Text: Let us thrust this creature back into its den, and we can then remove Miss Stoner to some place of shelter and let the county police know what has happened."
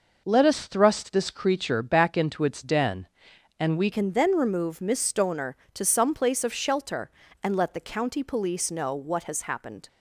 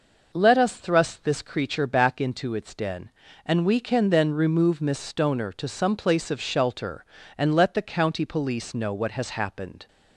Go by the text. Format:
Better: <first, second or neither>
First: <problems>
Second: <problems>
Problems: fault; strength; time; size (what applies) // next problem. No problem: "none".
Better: second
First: changes voice at "can"; from 3.9 s on; 5.9 s long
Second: none